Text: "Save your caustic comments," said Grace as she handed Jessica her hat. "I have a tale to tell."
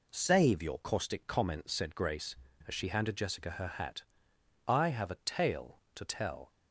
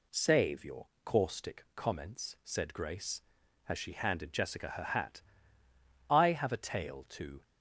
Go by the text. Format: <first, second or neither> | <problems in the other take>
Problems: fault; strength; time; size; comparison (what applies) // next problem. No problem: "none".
first | pauses between "your" and "caustic"; slight; at 0.8 s; 0.18 s long // stops before "tell"; at 7.4 s